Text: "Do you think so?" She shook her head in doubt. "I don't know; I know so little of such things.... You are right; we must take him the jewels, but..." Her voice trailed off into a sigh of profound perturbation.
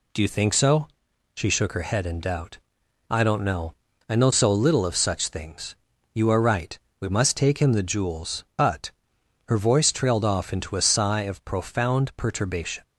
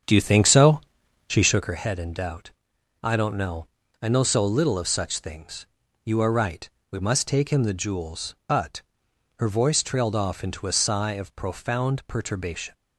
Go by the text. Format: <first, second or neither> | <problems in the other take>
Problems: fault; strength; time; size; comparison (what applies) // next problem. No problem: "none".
first | starts louder than the rest; strong; until 1.8 s; 8 dB